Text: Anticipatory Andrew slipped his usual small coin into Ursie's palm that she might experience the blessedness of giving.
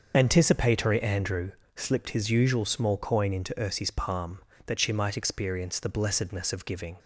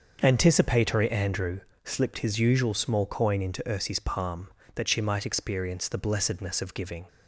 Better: second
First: loses the start of "Anticipatory"; at 0.1 s; 45 ms // starts louder than the rest; until 1.1 s; 6.5 dB // pauses between "Andrew" and "slipped"; slight; at 1.5 s; 0.26 s long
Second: starts louder than the rest; until 1.2 s; 6.5 dB // pauses between "Andrew" and "slipped"; slight; at 1.5 s; 0.26 s long

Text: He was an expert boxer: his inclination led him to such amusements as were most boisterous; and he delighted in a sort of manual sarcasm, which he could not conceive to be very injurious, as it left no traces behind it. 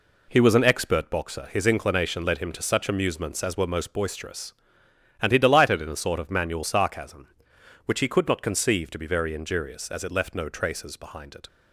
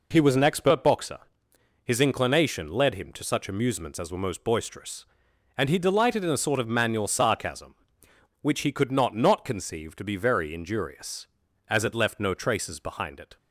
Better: first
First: none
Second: says "not" twice; at 9.1 s

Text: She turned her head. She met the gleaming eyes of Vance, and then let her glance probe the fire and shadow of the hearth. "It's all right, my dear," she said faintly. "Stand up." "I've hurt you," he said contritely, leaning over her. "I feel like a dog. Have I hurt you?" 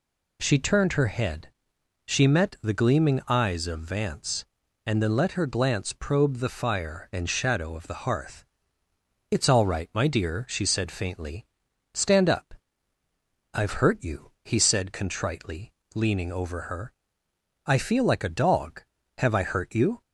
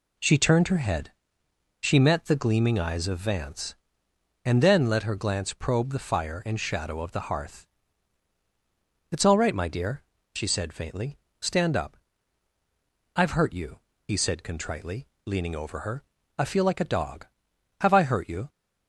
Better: neither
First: none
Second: none

